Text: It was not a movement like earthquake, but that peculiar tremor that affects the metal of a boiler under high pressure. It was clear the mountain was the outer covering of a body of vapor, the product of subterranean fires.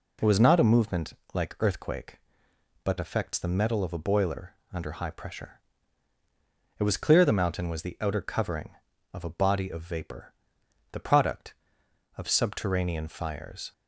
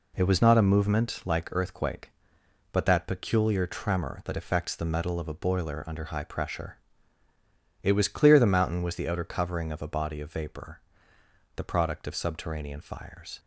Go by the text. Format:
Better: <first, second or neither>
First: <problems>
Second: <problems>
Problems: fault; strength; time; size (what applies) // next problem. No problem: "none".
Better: second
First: pauses between "movement" and "like"; slight; at 1.1 s; 0.18 s long // skips "that peculiar tremor that"; at 2.9 s // pauses between "boiler" and "under"; slight; at 4.5 s; 0.22 s long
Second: none